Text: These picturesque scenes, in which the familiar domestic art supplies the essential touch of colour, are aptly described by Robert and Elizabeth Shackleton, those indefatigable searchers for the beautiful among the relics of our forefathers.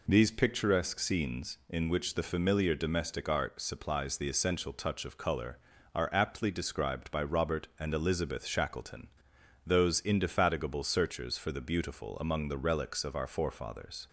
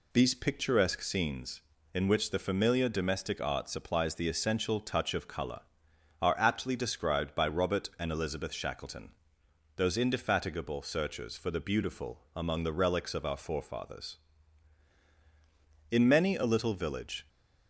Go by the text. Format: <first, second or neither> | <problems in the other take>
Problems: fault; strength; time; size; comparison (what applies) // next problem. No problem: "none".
first | goes on to say "In many a little village"; from 15.9 s on; 1.3 s long